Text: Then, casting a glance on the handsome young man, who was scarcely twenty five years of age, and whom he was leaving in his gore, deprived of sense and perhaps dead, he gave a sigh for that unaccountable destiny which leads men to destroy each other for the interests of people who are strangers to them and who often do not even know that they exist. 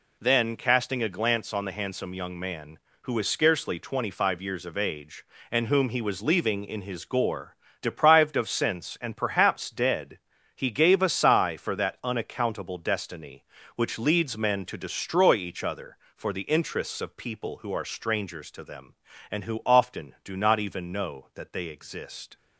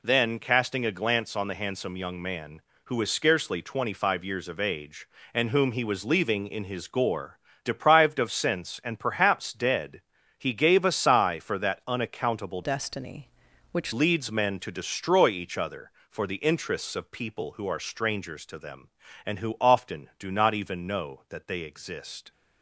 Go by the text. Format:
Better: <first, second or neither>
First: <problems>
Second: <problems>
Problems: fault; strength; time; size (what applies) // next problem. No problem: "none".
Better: first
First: none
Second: changes voice from "destiny" to "which"; from 12.6 to 13.9 s; 1.3 s long